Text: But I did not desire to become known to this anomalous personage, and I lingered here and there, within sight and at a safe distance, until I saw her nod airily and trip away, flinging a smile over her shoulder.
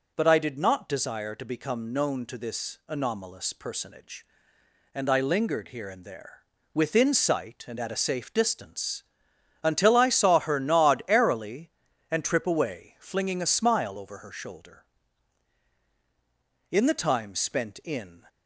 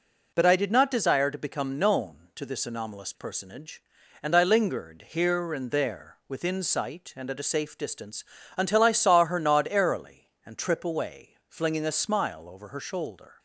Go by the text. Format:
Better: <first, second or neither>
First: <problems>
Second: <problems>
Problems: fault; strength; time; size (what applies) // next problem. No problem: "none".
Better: second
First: goes on to say "In the time spent in"; from 16.7 s on; 1.5 s long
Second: none